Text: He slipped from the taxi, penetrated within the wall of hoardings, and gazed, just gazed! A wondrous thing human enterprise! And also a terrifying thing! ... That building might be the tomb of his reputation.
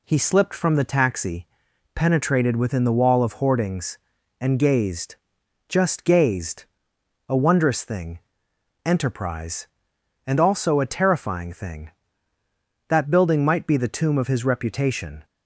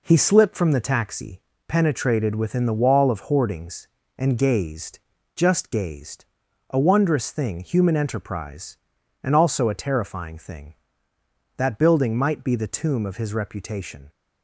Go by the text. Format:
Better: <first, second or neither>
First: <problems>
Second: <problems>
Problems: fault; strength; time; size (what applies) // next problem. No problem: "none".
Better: second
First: skips "human"; at 8.5 s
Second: none